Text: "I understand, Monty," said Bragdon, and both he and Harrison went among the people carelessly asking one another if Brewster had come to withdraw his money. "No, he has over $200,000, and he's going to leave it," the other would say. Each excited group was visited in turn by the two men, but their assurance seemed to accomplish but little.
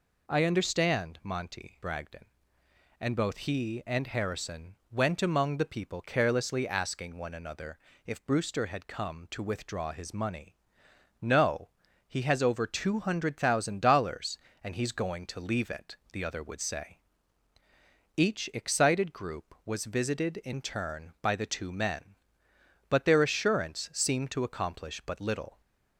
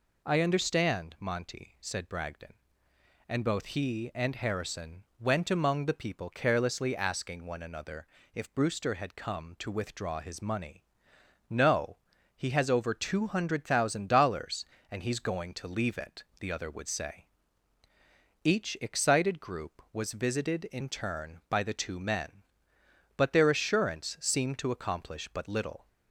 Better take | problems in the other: second | skips "said"; at 1.8 s // pauses between "Harrison" and "went"; slight; at 4.7 s; 0.16 s long; slight in the second // pauses between "another" and "if"; slight; at 7.7 s; 0.26 s long; slight in the second

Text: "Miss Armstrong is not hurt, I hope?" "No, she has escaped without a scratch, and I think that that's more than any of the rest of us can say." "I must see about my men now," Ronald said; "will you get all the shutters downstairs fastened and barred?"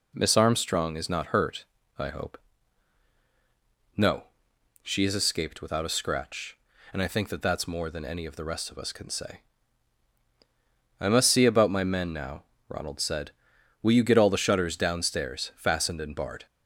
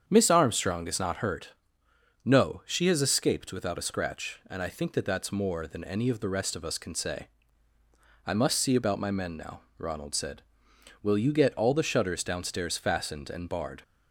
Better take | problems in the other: first | starts louder than the rest; strong; until 1.0 s; 8 dB // skips "I hope"; at 1.8 s

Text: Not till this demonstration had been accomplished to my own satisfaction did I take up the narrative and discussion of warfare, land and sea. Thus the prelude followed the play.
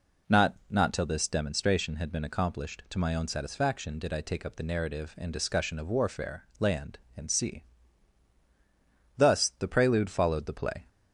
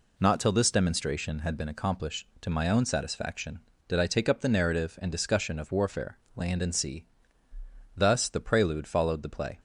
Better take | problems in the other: second | says "Not" twice; at 0.7 s

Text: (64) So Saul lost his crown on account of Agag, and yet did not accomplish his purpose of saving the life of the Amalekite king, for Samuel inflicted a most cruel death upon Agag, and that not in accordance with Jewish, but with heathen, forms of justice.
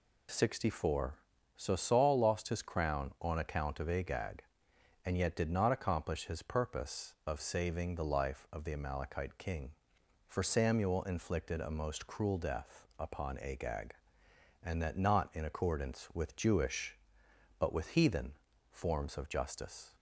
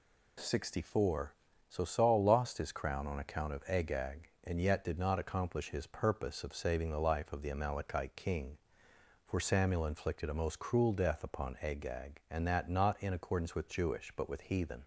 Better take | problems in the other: first | stops before "forms of justice"; at 14.8 s

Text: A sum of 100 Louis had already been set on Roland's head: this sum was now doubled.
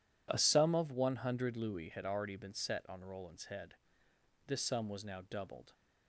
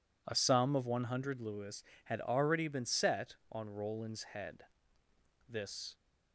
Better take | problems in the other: first | stops before "sum was now doubled"; at 5.9 s

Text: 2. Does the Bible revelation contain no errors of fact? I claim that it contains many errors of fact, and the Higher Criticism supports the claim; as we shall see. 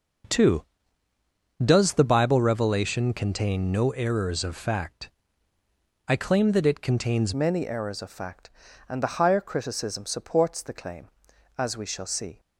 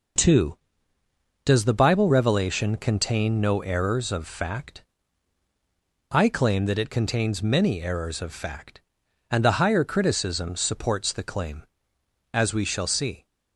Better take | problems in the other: second | changes voice at "many"; from 7.3 s on; 5.0 s long

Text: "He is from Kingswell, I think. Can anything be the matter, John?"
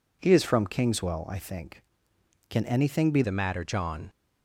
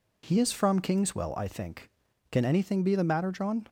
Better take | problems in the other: second | changes voice at "the"; from 3.2 s on; 0.8 s long

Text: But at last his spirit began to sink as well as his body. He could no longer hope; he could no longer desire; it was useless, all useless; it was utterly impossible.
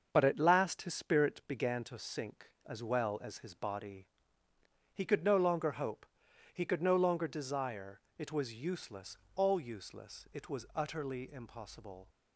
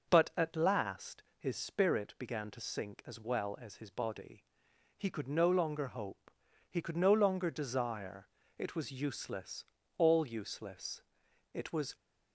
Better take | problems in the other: first | starts louder than the rest; until 1.1 s; 6 dB; also in the first // stops before "utterly impossible"; at 11.9 s

